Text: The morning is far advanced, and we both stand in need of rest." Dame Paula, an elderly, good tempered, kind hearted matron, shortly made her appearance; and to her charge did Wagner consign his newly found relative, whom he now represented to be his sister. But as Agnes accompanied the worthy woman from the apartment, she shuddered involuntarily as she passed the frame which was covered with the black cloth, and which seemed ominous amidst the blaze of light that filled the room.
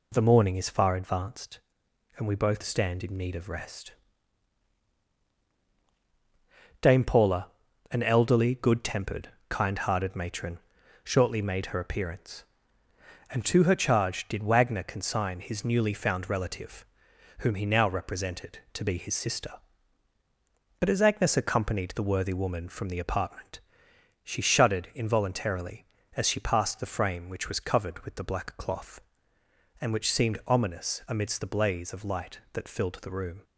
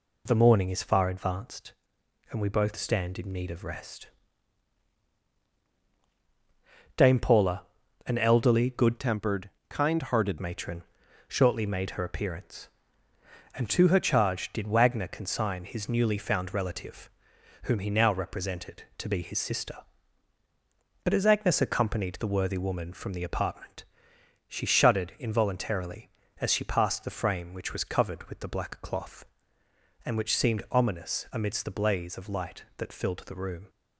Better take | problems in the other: first | changes voice from "tempered" to "hearted"; from 8.9 to 10.3 s; 1.4 s long

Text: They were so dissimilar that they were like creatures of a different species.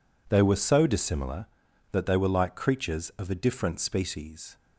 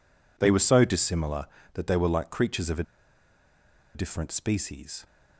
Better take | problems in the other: first | pauses between "a" and "different"; at 2.8 s; 1.1 s long

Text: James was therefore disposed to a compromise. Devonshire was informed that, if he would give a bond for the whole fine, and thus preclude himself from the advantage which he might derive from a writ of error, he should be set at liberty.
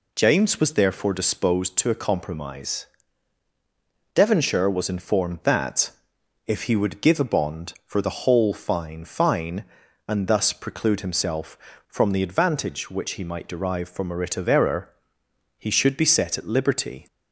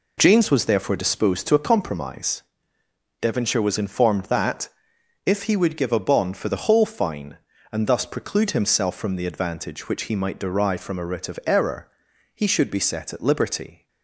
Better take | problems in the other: second | says "fine" twice; at 9.0 s

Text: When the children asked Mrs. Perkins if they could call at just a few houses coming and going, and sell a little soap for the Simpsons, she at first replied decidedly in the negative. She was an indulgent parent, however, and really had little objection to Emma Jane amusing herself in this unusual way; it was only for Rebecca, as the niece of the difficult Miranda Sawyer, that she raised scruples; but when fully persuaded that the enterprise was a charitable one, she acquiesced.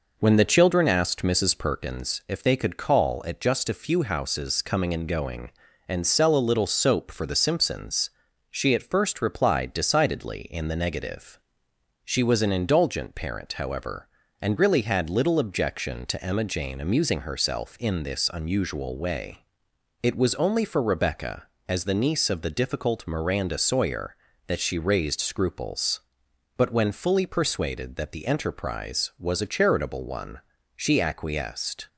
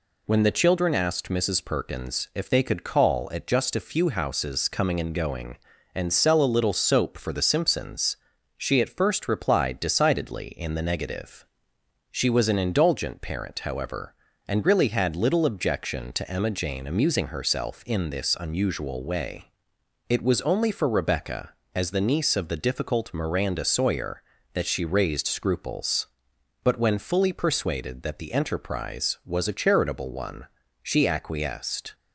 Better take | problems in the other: second | starts louder than the rest; noticeable; until 1.8 s; 5 dB

